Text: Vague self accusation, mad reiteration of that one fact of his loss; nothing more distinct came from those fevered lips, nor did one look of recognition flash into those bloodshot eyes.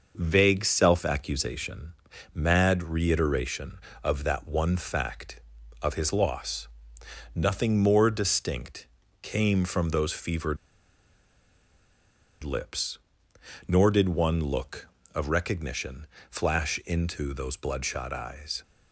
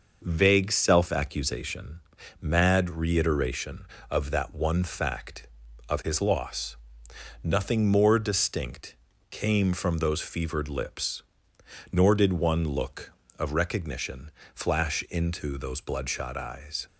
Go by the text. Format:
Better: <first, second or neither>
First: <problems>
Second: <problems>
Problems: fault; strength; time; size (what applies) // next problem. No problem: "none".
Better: second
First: pauses between "distinct" and "came"; slight; at 8.8 s; 0.34 s long // pauses between "fevered" and "lips"; strong; at 10.5 s; 1.8 s long // pauses between "recognition" and "flash"; slight; at 16.0 s; 0.24 s long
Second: pauses between "distinct" and "came"; slight; at 8.9 s; 0.34 s long // pauses between "recognition" and "flash"; slight; at 14.3 s; 0.24 s long